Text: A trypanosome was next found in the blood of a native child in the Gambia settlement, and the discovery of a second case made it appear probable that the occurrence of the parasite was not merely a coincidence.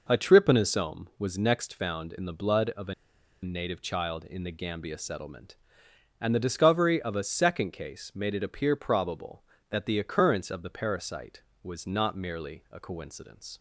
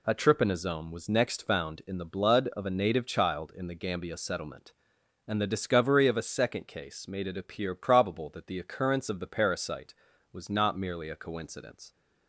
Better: second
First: pauses between "a" and "native"; noticeable; at 2.9 s; 0.50 s long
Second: none

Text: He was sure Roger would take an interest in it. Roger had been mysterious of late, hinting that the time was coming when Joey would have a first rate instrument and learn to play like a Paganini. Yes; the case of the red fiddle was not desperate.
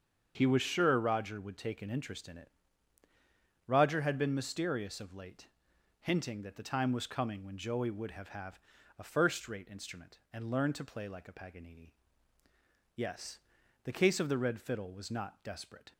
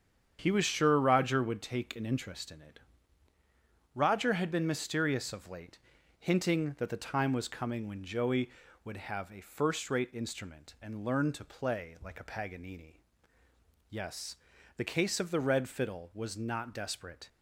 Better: second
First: starts louder than the rest; until 1.3 s; 7 dB // says "have" twice; at 8.2 s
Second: starts louder than the rest; strong; until 1.4 s; 8 dB

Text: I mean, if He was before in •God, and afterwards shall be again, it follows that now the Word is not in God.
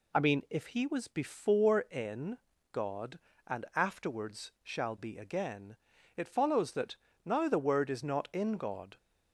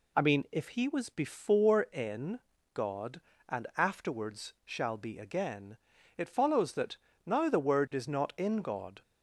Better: neither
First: pauses between "that" and "now"; slight; at 6.9 s; 0.30 s long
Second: pauses between "that" and "now"; slight; at 6.9 s; 0.30 s long

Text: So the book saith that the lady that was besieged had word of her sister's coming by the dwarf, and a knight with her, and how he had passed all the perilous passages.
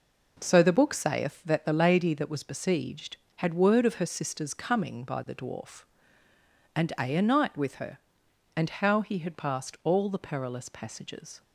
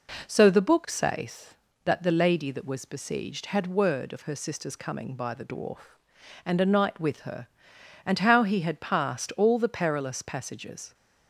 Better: second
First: says "a" twice; at 7.1 s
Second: none

